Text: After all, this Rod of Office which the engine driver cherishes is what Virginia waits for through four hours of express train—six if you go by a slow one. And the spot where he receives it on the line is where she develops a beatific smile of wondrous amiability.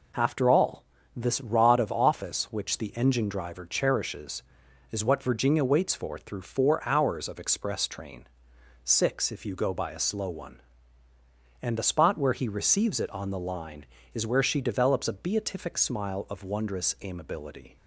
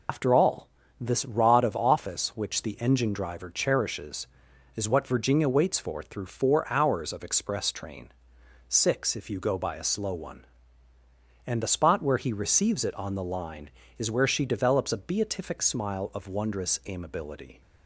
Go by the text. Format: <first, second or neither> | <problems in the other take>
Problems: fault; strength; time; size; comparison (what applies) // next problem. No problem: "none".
first | loses the start of "After"; at 0.0 s; 110 ms